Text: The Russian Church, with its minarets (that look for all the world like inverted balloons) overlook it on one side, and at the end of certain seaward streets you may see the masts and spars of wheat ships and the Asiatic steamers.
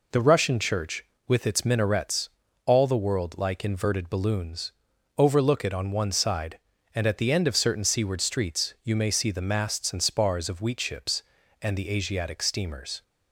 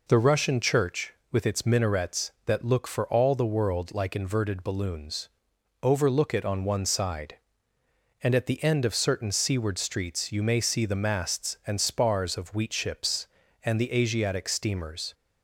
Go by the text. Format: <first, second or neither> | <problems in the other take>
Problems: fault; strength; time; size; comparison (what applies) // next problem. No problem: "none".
second | skips "that look for"; at 2.4 s